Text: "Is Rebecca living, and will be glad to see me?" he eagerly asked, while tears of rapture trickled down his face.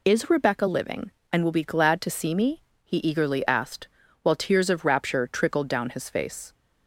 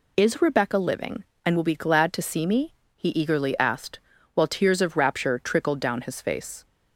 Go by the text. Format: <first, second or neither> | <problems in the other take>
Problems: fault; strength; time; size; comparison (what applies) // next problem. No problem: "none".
neither | none